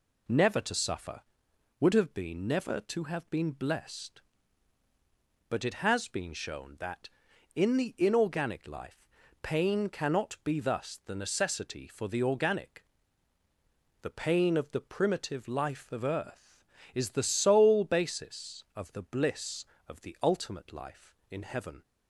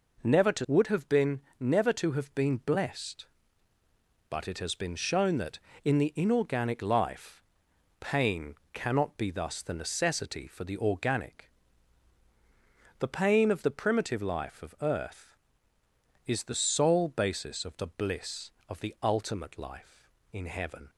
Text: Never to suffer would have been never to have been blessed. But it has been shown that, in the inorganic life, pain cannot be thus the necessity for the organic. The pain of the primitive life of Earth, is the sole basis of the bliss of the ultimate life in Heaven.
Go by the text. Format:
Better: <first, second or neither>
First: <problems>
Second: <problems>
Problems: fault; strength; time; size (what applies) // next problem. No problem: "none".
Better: first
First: none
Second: skips "suffer"; at 0.6 s // pauses between "been" and "never"; slight; at 1.4 s; 0.18 s long // pauses between "pain" and "cannot"; slight; at 8.5 s; 0.18 s long